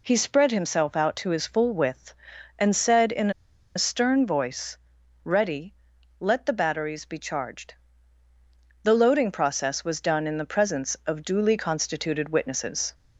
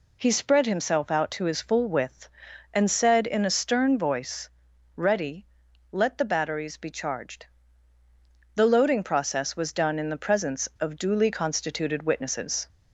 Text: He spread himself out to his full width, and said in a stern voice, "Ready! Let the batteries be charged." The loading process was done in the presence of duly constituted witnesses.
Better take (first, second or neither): second